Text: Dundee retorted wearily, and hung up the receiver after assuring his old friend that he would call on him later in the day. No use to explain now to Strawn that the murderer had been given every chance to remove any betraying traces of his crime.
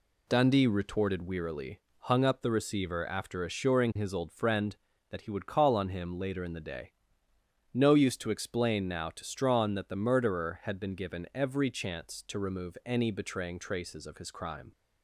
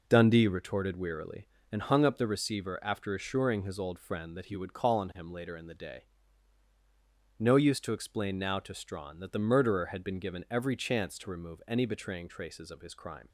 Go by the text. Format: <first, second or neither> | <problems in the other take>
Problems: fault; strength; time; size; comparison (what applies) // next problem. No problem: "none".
second | skips "and"; at 1.9 s